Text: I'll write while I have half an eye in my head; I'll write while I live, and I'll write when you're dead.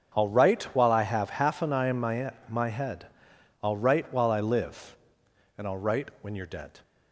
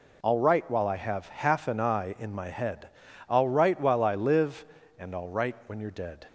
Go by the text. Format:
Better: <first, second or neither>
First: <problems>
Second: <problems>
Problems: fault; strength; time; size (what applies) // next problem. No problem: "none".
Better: second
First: starts louder than the rest; strong; until 1.2 s; 8 dB // says "my" twice; at 2.4 s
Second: none